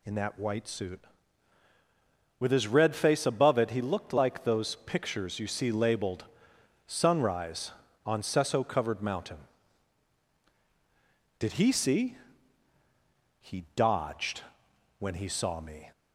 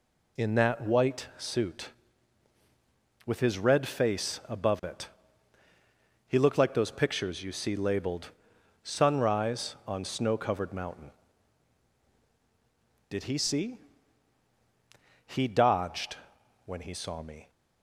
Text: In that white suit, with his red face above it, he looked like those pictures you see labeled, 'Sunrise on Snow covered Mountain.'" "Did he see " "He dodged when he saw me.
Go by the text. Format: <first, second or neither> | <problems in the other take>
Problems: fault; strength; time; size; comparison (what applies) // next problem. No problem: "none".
second | says "Sesso" for "Snow"; at 8.2 s // pauses between "dodged" and "when"; noticeable; at 14.4 s; 0.56 s long; noticeable in the second